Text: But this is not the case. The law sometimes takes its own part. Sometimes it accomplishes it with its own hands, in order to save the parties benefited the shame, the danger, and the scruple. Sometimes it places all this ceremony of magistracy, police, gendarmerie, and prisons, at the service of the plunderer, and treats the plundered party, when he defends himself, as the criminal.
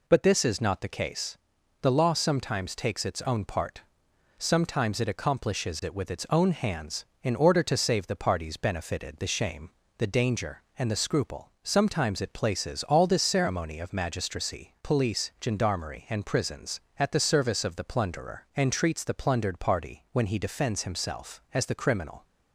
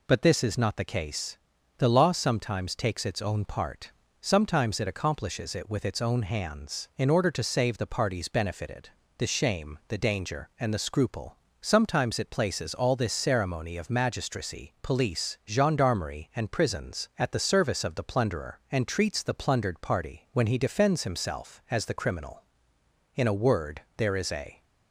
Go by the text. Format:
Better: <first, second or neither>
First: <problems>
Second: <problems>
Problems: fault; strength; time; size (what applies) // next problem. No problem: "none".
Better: first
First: none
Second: pauses between "benefited" and "the"; slight; at 8.8 s; 0.28 s long // goes on to say "In a word there is a"; from 23.1 s on; 1.5 s long